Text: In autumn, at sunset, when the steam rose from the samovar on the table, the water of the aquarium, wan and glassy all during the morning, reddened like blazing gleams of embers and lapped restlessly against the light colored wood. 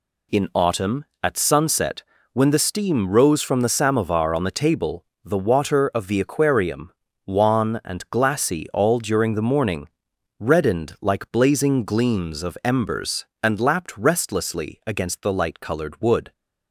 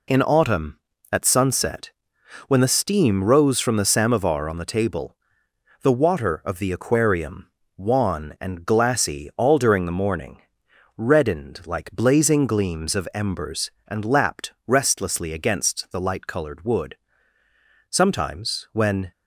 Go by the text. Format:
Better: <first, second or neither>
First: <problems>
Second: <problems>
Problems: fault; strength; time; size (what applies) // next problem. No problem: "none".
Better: first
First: none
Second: goes on to say "Sometimes when"; noticeable; from 17.9 s on; 1.2 s long